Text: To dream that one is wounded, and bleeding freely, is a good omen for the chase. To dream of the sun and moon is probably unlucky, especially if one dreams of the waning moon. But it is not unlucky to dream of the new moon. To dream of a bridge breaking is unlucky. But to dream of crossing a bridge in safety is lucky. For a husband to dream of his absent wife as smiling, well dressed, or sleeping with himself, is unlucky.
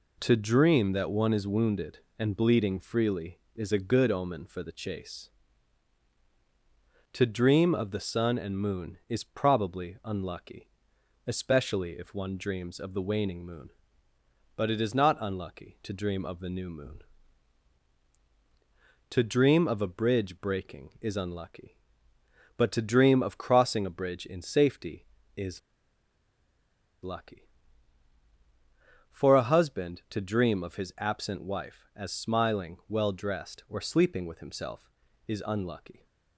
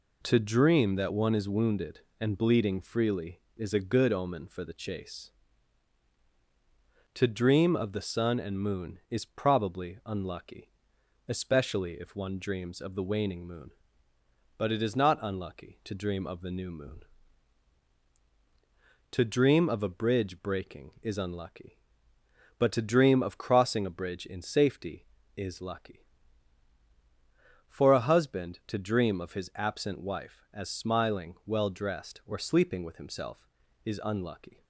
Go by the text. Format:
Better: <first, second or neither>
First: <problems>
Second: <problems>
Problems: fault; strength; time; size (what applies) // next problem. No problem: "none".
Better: second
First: pauses between "is" and "lucky"; strong; at 25.5 s; 1.4 s long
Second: none